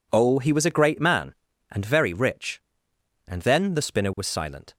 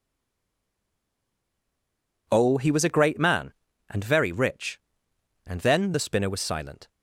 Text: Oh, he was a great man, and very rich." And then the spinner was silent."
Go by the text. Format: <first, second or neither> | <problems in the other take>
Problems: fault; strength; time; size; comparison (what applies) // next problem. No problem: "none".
first | stays silent before the first word; until 2.2 s; 2.2 s long